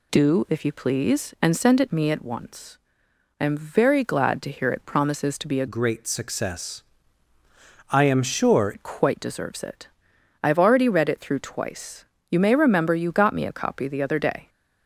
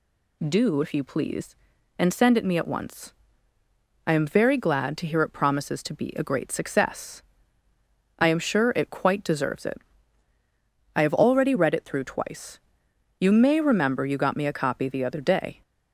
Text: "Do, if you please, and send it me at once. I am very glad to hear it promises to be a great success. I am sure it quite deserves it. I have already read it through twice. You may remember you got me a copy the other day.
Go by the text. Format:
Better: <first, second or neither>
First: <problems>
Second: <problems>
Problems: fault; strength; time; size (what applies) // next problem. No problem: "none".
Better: second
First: changes voice from "great" to "sure"; from 5.6 to 8.7 s; 3.1 s long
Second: none